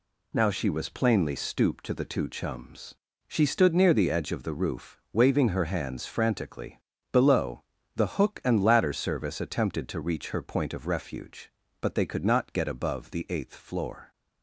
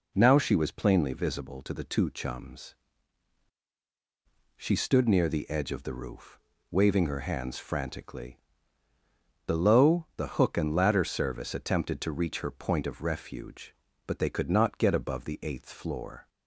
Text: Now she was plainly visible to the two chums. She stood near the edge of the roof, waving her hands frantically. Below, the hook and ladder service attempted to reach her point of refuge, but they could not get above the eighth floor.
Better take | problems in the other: second | says "stooped" for "visible"; at 1.3 s

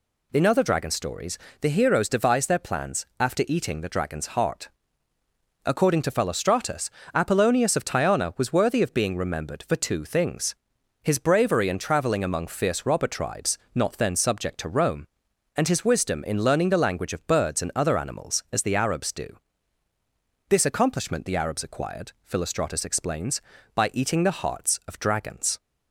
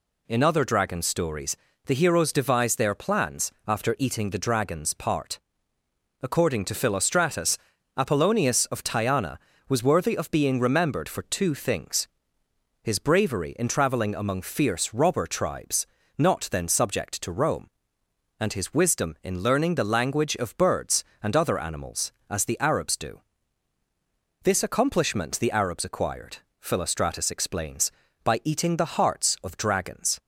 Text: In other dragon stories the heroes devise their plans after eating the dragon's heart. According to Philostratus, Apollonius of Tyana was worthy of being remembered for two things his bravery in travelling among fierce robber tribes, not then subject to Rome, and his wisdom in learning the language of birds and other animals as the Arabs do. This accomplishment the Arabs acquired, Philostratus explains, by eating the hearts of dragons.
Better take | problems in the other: first | pauses between "stories" and "the"; slight; at 1.5 s; 0.30 s long; slight in the first // pauses between "plans" and "after"; slight; at 3.5 s; 0.16 s long // says "part" for "heart"; at 4.9 s // pauses between "things" and "his"; noticeable; at 12.0 s; 0.74 s long; noticeable in the first

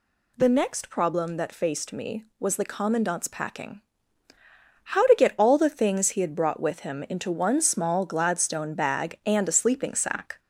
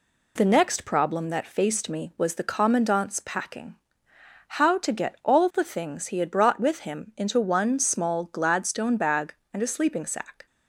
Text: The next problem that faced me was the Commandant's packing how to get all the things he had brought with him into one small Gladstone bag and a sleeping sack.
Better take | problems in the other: second | gets louder; slight; throughout; 2.5 dB // pauses between "packing" and "how"; at 3.8 s; 1.0 s long; noticeable in the second

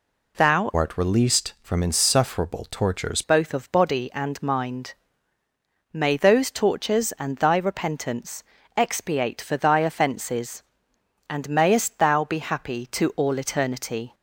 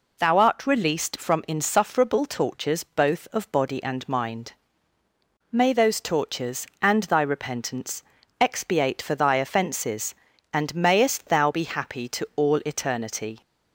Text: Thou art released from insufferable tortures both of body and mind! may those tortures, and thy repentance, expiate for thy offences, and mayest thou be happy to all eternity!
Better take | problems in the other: second | changes voice from "art" to "tortures"; from 0.7 to 3.2 s; 2.5 s long

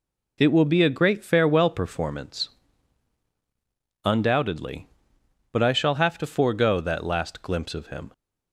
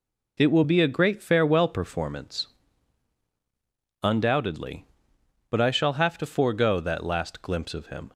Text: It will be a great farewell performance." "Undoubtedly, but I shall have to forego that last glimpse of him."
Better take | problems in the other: neither | none

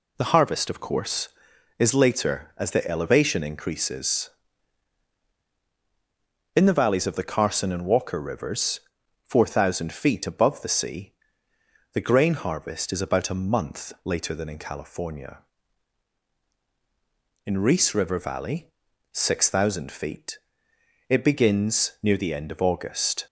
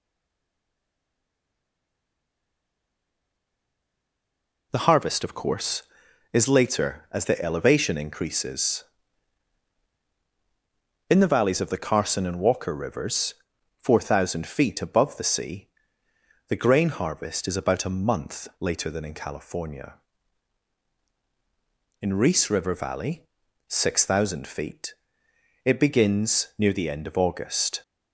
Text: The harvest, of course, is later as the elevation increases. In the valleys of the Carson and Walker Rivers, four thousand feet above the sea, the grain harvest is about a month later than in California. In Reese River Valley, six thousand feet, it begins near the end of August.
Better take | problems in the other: first | stays silent before the first word; strong; until 4.7 s; 4.7 s long

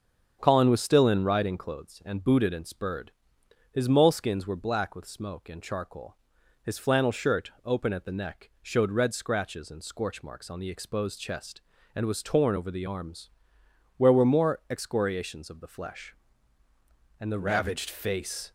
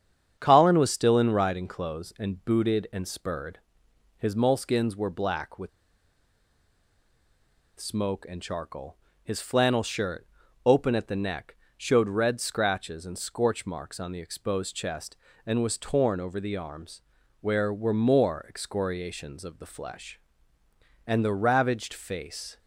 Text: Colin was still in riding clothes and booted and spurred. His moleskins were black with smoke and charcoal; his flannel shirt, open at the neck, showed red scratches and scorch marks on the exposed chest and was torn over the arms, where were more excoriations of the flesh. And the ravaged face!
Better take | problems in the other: first | starts louder than the rest; strong; until 1.3 s; 8 dB; strong in the first // pauses between "with" and "smoke"; strong; at 5.6 s; 2.1 s long

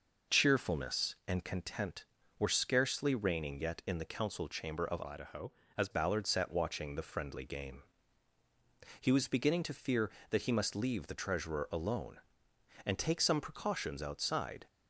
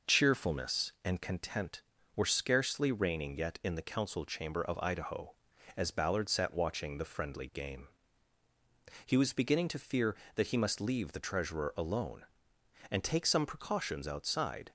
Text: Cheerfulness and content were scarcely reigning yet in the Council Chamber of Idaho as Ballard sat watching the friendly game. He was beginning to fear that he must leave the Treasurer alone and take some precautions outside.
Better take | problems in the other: second | changes voice from "Idaho" to "as"; from 5.0 to 5.8 s; 0.8 s long

